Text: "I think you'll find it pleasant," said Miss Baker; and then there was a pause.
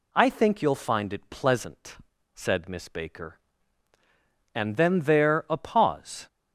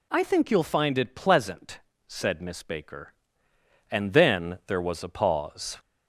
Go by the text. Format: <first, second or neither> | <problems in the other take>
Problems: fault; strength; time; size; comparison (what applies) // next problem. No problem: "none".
second | skips "was"; at 5.4 s